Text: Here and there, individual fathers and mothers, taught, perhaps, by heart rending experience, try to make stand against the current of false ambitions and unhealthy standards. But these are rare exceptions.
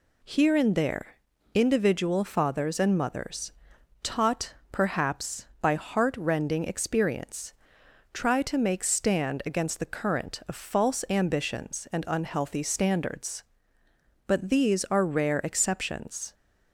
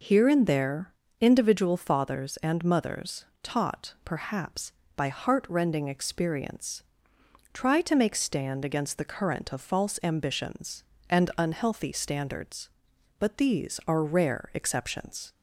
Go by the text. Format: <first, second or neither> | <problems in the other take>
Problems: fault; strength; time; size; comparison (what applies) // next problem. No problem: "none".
neither | none